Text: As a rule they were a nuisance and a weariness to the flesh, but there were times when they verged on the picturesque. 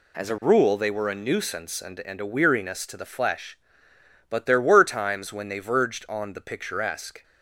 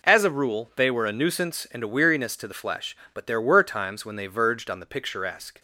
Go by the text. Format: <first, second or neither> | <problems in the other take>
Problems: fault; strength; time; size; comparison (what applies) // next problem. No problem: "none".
second | says "and" twice; at 2.0 s